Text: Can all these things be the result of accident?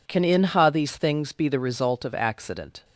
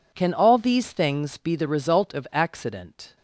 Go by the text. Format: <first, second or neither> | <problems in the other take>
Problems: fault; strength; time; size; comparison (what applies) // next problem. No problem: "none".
second | says "inha" for "all"; at 0.2 s